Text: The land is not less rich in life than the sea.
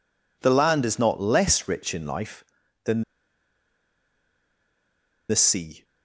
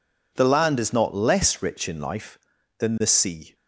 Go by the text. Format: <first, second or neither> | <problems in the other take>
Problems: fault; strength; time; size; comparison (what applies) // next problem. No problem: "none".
second | pauses between "than" and "the"; strong; at 3.0 s; 2.2 s long